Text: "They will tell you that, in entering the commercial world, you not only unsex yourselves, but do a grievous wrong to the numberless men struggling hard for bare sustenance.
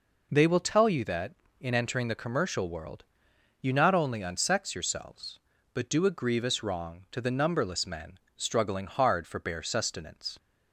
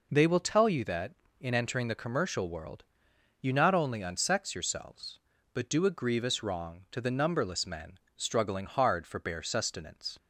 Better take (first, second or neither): neither